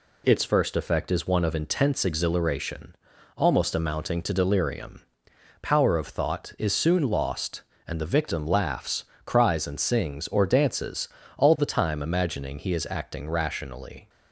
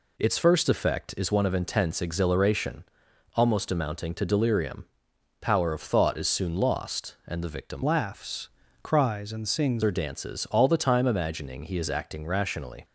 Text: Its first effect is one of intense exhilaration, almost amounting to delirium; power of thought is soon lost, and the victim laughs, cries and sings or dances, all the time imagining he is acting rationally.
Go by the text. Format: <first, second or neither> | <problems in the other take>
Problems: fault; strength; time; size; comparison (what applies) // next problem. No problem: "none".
first | changes voice from "laughs" to "sings"; from 7.8 to 9.8 s; 2.0 s long